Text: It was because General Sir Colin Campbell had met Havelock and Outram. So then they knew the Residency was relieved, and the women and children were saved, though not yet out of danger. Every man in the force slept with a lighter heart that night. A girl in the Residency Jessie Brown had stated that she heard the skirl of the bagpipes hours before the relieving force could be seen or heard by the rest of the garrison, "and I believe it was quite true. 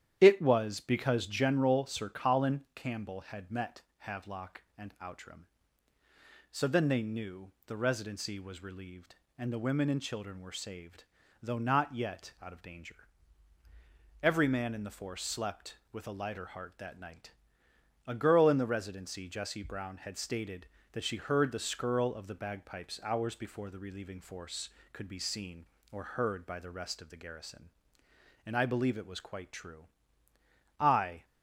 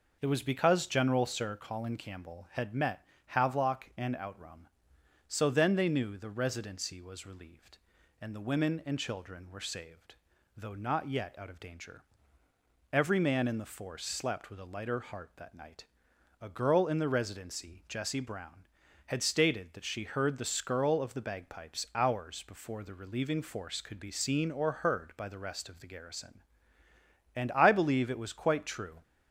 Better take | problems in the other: second | starts louder than the rest; strong; until 1.2 s; 10.5 dB // pauses between "met" and "Havelock"; slight; at 3.8 s; 0.16 s long; slight in the second // pauses between "knew" and "the"; slight; at 7.5 s; 0.16 s long // goes on to say "I"; slight; from 30.8 s on; 0.44 s long

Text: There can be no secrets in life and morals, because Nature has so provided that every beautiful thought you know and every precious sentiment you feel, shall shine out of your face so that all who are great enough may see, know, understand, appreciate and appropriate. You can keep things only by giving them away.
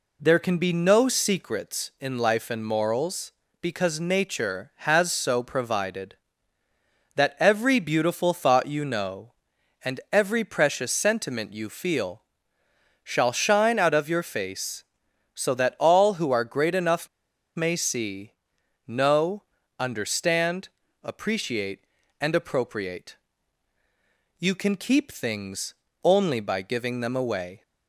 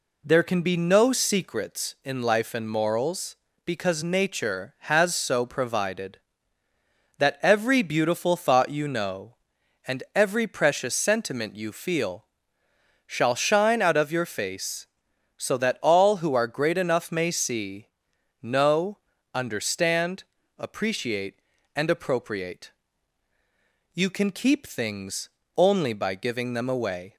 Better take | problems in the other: second | pauses between "enough" and "may"; noticeable; at 17.0 s; 0.48 s long // pauses between "things" and "only"; slight; at 25.7 s; 0.30 s long; slight in the second

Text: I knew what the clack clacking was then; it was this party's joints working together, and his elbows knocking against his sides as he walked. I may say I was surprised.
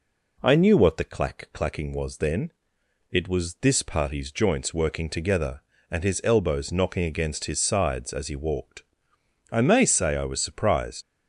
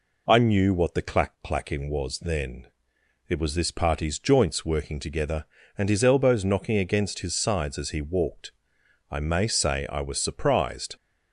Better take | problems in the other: second | leaves "surprised" unfinished; at 11.0 s; 55 ms

